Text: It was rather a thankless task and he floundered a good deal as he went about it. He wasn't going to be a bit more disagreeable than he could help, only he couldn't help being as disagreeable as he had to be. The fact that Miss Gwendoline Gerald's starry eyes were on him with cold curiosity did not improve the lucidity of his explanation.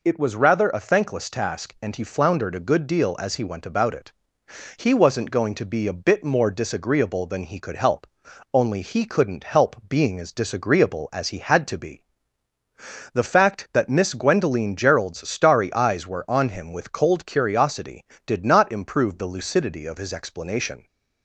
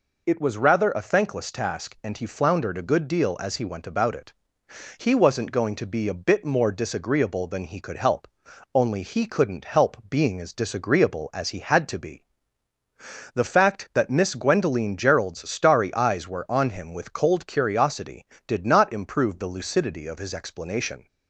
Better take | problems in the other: neither | none

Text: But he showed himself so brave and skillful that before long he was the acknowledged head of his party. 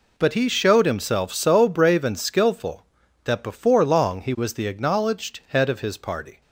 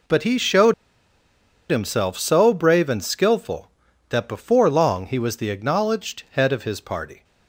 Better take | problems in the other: first | pauses between "showed" and "himself"; noticeable; at 0.7 s; 0.97 s long

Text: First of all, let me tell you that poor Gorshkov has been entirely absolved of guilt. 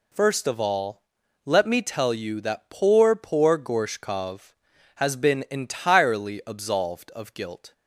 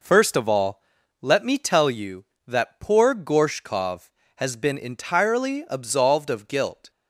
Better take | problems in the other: second | says "poor" twice; at 3.1 s

